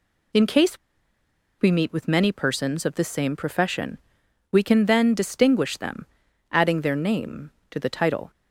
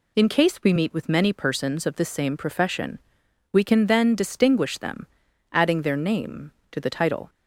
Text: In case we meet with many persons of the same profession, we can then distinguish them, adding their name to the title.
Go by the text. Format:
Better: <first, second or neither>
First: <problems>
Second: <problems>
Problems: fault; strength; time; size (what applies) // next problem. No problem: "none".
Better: second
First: pauses between "case" and "we"; noticeable; at 0.7 s; 0.84 s long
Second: none